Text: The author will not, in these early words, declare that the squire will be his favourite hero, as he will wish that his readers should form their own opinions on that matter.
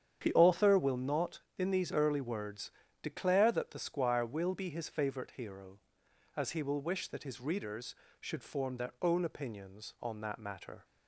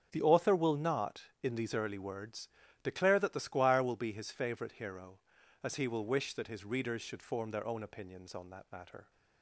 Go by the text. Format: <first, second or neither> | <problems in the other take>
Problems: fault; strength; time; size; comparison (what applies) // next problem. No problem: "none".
neither | starts louder than the rest; strong; the same in both